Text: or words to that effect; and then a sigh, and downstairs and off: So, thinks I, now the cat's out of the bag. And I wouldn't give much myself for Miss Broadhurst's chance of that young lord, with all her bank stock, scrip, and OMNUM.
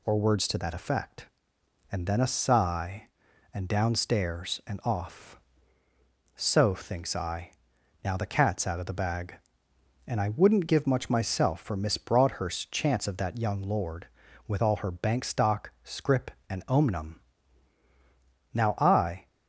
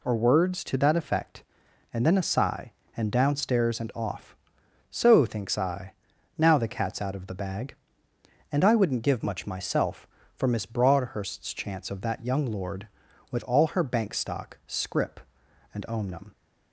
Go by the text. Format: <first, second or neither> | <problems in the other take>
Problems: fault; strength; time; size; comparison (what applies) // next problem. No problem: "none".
second | goes on to say "Now I"; noticeable; from 18.5 s on; 0.74 s long